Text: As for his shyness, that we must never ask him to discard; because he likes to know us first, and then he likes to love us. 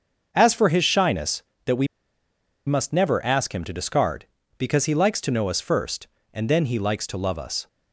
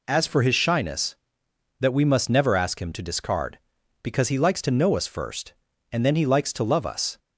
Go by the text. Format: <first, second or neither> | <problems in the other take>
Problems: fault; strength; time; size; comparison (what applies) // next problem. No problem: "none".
second | starts louder than the rest; until 1.3 s; 6.5 dB // pauses between "we" and "must"; noticeable; at 1.8 s; 0.82 s long